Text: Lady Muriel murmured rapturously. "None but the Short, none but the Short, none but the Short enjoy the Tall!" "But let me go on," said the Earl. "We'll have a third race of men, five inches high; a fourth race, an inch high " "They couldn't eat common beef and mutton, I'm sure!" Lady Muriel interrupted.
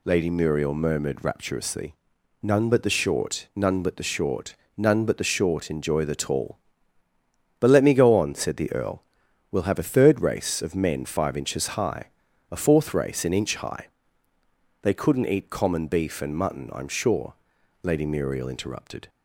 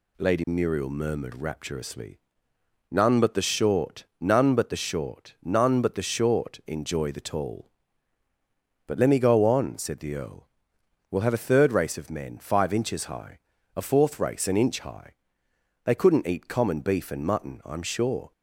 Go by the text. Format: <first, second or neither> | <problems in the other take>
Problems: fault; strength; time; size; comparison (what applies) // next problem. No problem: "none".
first | stops before "Lady Muriel interrupted"; at 18.3 s